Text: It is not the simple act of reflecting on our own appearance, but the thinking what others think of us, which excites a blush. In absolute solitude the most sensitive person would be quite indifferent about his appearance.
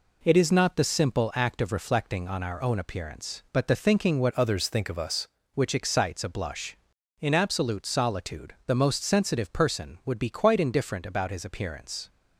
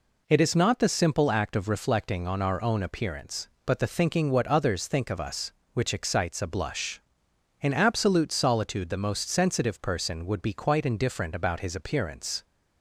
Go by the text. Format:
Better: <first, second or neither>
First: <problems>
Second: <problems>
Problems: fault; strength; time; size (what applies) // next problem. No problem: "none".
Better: second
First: changes voice from "others" to "us"; from 4.3 to 5.2 s; 0.9 s long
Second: none